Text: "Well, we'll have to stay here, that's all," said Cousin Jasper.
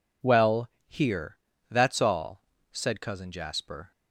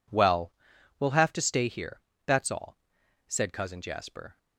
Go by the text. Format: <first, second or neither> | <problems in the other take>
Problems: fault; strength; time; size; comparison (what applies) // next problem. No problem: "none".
second | skips "we'll have to stay"; at 0.7 s